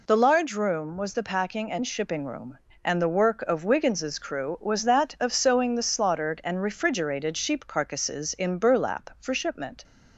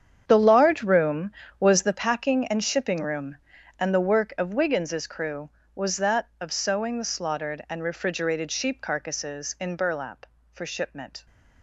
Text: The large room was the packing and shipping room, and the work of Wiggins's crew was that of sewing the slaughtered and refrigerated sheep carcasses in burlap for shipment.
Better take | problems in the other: first | gets quieter; strong; throughout; 13.5 dB

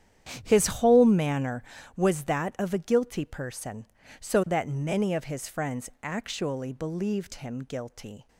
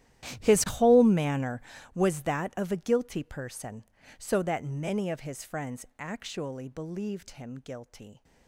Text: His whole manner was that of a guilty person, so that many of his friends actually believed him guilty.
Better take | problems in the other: first | gets quieter; strong; throughout; 19 dB // starts louder than the rest; strong; until 1.4 s; 12.5 dB; strong in the first

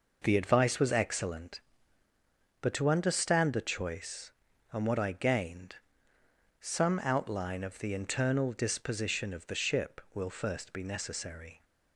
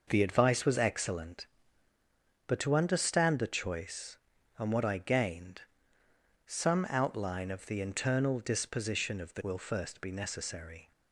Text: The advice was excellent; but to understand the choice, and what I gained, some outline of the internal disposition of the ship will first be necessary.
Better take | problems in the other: first | skips "ship"; at 9.4 s

